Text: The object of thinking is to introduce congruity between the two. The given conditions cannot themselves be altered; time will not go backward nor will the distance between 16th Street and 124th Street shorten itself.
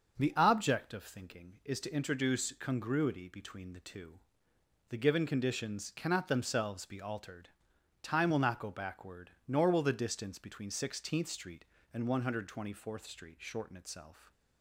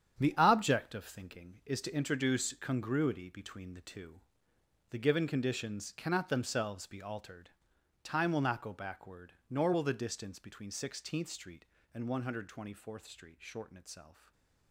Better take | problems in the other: first | gets quieter; strong; throughout; 9.5 dB // stays silent after the last word; slight; from 14.1 s on; 0.6 s long

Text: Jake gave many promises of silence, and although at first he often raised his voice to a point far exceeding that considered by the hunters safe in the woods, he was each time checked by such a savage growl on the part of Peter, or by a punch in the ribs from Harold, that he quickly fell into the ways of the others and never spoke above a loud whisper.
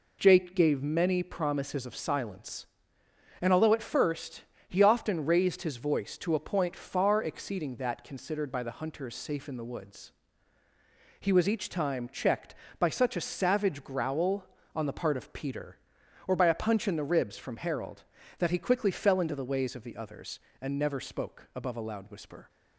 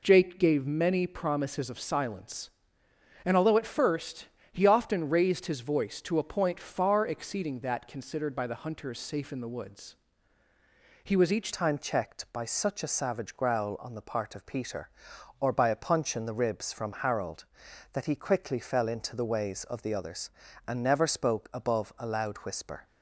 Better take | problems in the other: first | pauses between "first" and "he"; slight; at 4.2 s; 0.26 s long; slight in the first // changes voice at "time"; from 11.5 s on; 11.3 s long

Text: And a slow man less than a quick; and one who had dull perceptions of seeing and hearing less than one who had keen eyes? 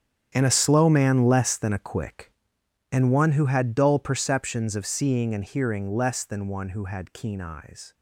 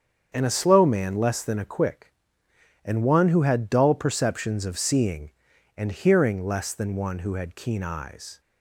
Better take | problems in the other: second | gets quieter; strong; throughout; 14.5 dB // starts louder than the rest; strong; until 1.3 s; 9 dB; strong in the second

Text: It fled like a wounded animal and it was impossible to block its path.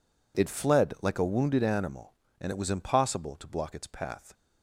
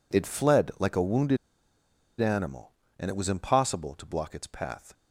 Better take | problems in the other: first | pauses between "wounded" and "animal"; noticeable; at 1.3 s; 0.84 s long

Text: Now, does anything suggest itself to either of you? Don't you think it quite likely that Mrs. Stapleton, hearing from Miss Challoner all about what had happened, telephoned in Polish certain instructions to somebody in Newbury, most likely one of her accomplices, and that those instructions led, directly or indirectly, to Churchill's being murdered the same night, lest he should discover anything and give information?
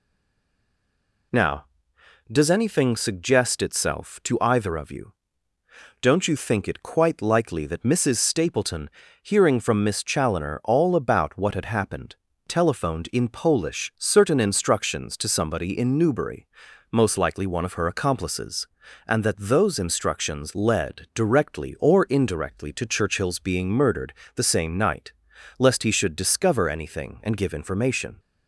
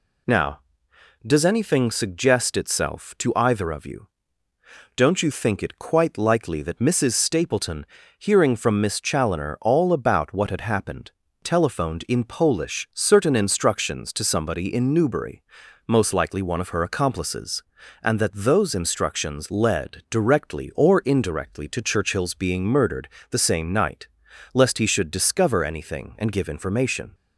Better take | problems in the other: second | stays silent before the first word; noticeable; until 1.3 s; 1.3 s long // pauses between "murdered" and "the"; slight; at 24.1 s; 0.22 s long; slight in the second

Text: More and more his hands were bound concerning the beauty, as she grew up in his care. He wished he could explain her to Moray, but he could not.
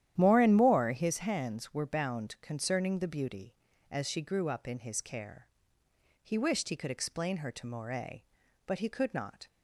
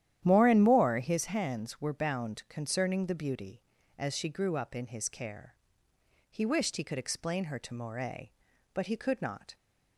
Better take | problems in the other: neither | starts louder than the rest; strong; the same in both

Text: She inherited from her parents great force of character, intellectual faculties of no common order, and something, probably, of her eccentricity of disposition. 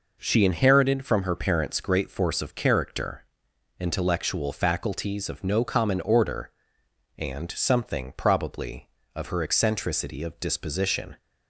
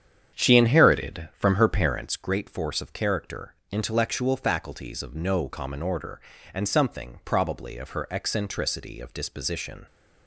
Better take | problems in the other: first | starts louder than the rest; strong; until 2.1 s; 8.5 dB

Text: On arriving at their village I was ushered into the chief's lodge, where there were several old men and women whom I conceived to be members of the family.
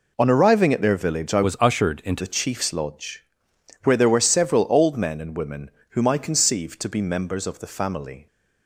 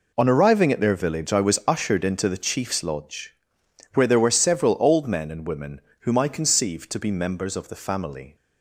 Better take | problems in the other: second | changes voice from "was" to "into"; from 1.4 to 2.2 s; 0.8 s long // pauses between "women" and "whom"; slight; at 5.7 s; 0.20 s long; slight in the second

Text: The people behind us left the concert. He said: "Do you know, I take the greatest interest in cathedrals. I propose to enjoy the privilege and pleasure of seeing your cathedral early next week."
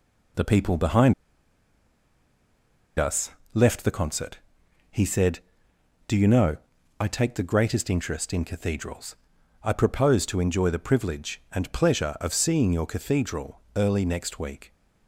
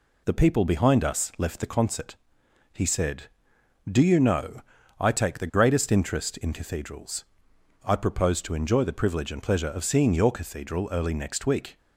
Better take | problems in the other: second | pauses between "behind" and "us"; strong; at 1.1 s; 1.8 s long // pauses between "us" and "left"; slight; at 3.3 s; 0.24 s long // pauses between "cathedral" and "early"; slight; at 13.6 s; 0.16 s long

